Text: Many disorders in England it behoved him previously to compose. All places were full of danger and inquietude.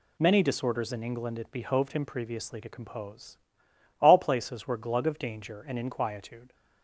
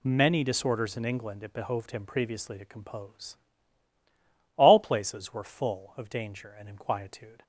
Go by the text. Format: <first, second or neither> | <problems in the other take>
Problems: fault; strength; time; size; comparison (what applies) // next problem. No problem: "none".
second | says "glug" for "full"; at 4.7 s